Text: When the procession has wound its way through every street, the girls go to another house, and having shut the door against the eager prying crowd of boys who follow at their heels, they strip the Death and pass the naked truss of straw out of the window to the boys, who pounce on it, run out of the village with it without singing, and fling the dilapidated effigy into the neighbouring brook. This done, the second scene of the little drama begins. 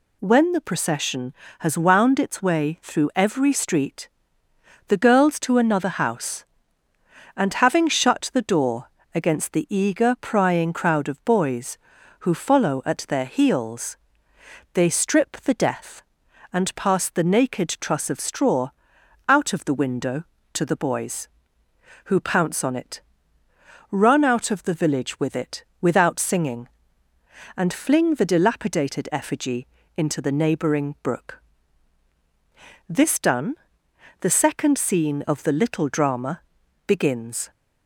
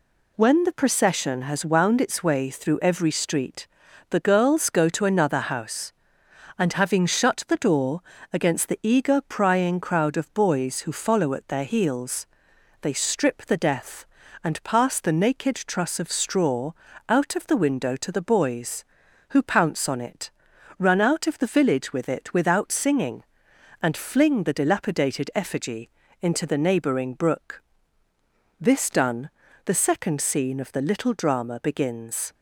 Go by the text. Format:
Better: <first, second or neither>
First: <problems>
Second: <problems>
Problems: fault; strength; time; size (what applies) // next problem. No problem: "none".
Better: second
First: skips "go"; at 5.3 s // pauses between "door" and "against"; slight; at 8.8 s; 0.24 s long // pauses between "straw" and "out"; noticeable; at 18.7 s; 0.54 s long // pauses between "it" and "without"; slight; at 25.6 s; 0.16 s long // pauses between "effigy" and "into"; slight; at 29.6 s; 0.30 s long // pauses between "drama" and "begins"; noticeable; at 36.3 s; 0.46 s long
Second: pauses between "door" and "against"; slight; at 8.0 s; 0.30 s long // pauses between "straw" and "out"; slight; at 16.7 s; 0.36 s long // pauses between "effigy" and "into"; slight; at 25.8 s; 0.32 s long